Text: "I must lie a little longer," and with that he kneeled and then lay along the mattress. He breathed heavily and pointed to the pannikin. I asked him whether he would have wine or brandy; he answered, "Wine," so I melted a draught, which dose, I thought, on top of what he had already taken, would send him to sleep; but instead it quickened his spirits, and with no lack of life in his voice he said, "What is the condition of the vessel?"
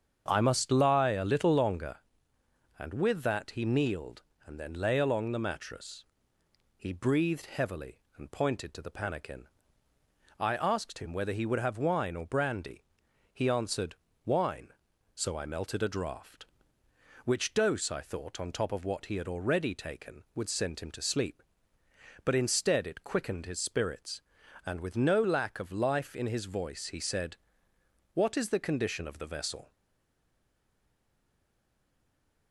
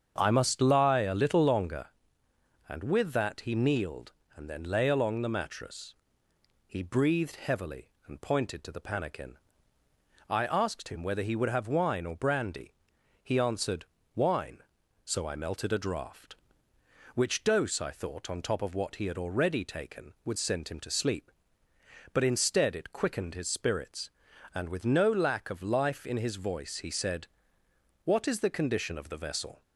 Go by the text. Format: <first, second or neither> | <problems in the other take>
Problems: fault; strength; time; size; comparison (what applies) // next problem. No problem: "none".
second | starts louder than the rest; strong; until 1.2 s; 7.5 dB; strong in the second // stays silent after the last word; strong; from 29.7 s on; 2.8 s long